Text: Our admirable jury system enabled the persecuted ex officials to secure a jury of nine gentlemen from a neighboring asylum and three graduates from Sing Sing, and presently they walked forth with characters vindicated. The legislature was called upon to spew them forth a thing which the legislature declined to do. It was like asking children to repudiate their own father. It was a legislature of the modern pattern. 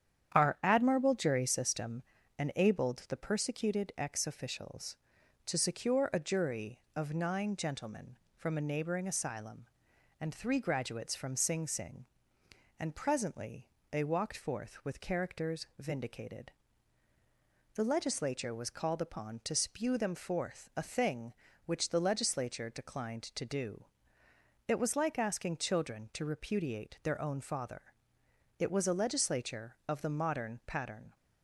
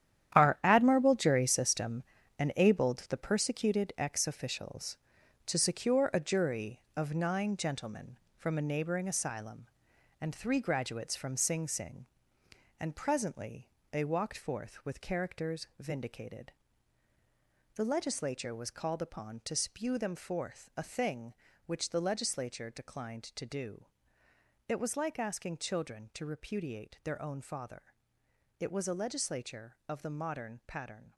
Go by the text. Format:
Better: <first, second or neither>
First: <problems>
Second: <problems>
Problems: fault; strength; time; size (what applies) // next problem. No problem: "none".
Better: first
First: starts louder than the rest; strong; until 1.4 s; 9 dB // pauses between "system" and "enabled"; at 2.0 s; 0.38 s long // pauses between "presently" and "they"; slight; at 13.6 s; 0.24 s long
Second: gets quieter; strong; throughout; 10.5 dB // starts louder than the rest; strong; until 1.4 s; 10.5 dB // pauses between "system" and "enabled"; at 2.0 s; 0.38 s long // pauses between "presently" and "they"; slight; at 13.6 s; 0.24 s long